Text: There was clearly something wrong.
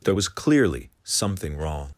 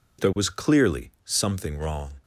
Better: second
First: leaves "wrong" unfinished; at 1.9 s; 80 ms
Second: none

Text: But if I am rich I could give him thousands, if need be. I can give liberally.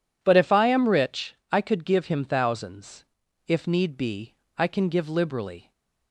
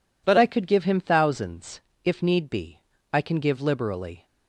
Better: first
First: none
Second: skips "if I am rich"; at 0.3 s

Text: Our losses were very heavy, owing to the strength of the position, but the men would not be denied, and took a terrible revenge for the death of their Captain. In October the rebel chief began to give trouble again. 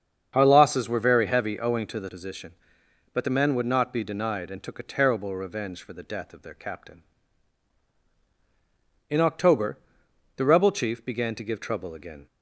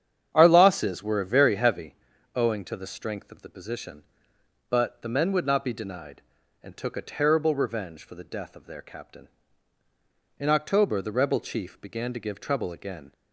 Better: second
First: starts louder than the rest; strong; until 1.3 s; 7.5 dB // skips "strength of the"; at 2.0 s // pauses between "October" and "the"; noticeable; at 9.7 s; 0.58 s long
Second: starts louder than the rest; strong; until 1.3 s; 9 dB

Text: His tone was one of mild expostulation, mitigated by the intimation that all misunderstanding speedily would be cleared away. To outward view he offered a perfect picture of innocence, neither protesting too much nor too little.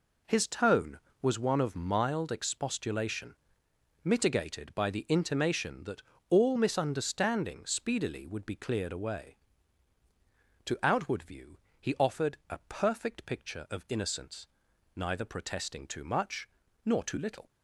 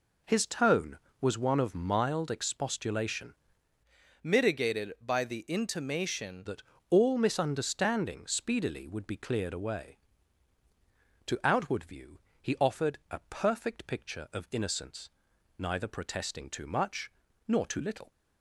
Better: first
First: pauses between "that" and "all"; slight; at 6.0 s; 0.28 s long // pauses between "view" and "he"; slight; at 11.5 s; 0.20 s long // pauses between "much" and "nor"; at 16.4 s; 0.38 s long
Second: changes voice from "mitigated" to "intimation"; from 4.2 to 6.4 s; 2.2 s long // pauses between "that" and "all"; slight; at 6.6 s; 0.28 s long // pauses between "view" and "he"; slight; at 12.2 s; 0.20 s long // pauses between "much" and "nor"; at 17.1 s; 0.38 s long

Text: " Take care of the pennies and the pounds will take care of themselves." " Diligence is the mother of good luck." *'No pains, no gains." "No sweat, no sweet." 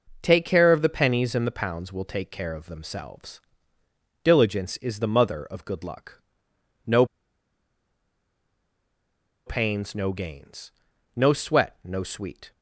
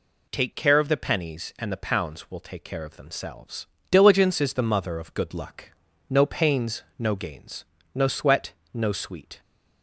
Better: second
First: pauses between "No" and "pains"; strong; at 7.0 s; 2.4 s long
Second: none

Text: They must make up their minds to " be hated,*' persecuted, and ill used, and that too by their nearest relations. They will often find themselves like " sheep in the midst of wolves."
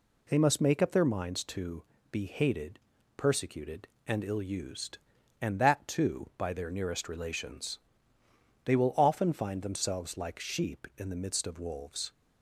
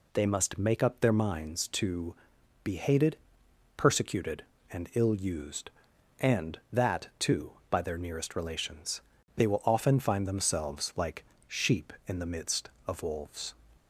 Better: neither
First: none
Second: none

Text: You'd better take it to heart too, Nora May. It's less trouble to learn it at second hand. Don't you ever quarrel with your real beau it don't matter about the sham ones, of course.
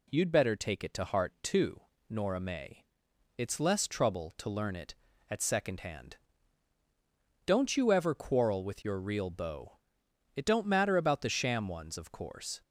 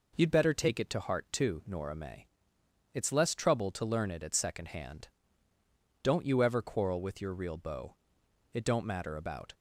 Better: first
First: pauses between "beau" and "it"; noticeable; at 9.7 s; 0.62 s long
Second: pauses between "beau" and "it"; noticeable; at 7.9 s; 0.58 s long // stops before "the sham ones of course"; at 9.5 s

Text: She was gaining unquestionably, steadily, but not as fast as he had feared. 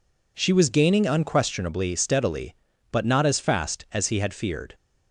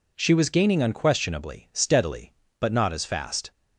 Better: first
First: none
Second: stops before "as he had feared"; at 3.5 s

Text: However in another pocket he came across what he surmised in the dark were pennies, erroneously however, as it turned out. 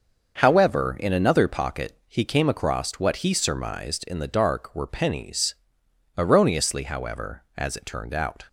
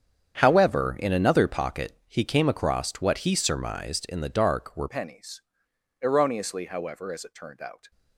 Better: first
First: starts louder than the rest; until 1.3 s; 6 dB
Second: starts louder than the rest; strong; until 1.3 s; 8 dB // changes voice at "pennies"; from 4.8 s on; 3.1 s long

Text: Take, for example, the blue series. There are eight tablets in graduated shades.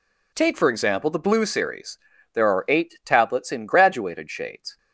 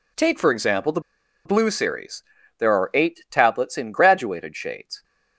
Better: first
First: none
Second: pauses between "the" and "blue"; at 0.9 s; 0.45 s long

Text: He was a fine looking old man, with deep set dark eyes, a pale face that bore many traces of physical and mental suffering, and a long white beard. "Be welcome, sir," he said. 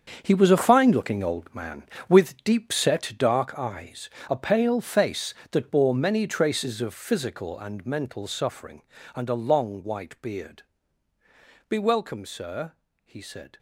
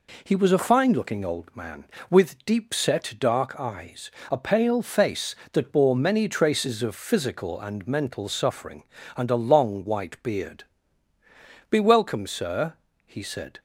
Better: second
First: gets quieter; strong; throughout; 11 dB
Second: none

